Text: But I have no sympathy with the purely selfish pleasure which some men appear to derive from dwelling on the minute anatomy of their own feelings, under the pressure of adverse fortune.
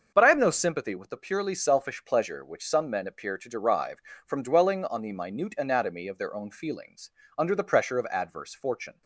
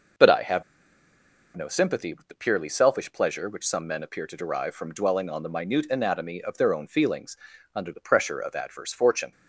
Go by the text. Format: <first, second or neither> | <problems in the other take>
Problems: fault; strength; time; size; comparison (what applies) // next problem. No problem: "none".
first | starts louder than the rest; noticeable; until 2.1 s; 6 dB; also in the first // pauses between "have" and "no"; noticeable; at 0.6 s; 0.92 s long